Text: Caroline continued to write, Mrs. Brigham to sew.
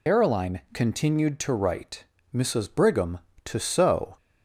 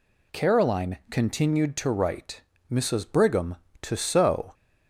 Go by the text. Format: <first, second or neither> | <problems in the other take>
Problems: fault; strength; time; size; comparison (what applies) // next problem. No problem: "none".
second | loses the start of "Caroline"; at 0.0 s; 120 ms